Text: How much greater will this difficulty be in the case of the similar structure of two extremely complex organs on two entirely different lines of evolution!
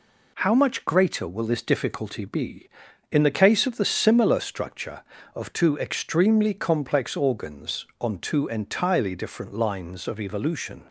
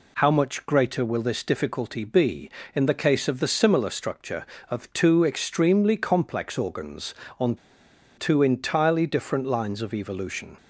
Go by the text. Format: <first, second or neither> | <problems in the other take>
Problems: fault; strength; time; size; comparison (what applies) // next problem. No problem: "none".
first | pauses between "on" and "two"; noticeable; at 7.5 s; 0.60 s long